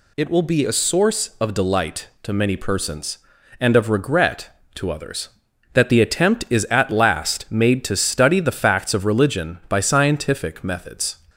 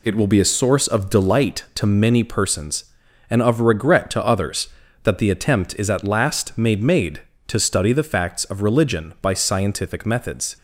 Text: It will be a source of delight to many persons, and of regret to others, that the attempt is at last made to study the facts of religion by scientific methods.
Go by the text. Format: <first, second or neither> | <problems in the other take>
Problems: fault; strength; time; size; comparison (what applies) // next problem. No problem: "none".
first | says "made" twice; at 6.8 s